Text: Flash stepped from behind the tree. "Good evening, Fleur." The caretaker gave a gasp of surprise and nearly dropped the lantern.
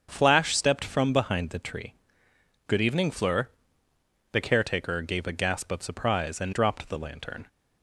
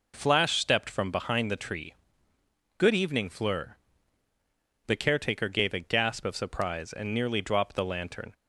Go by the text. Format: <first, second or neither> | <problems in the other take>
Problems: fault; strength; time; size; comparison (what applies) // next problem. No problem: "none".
second | starts louder than the rest; strong; until 1.1 s; 7 dB // skips "nearly"; at 6.5 s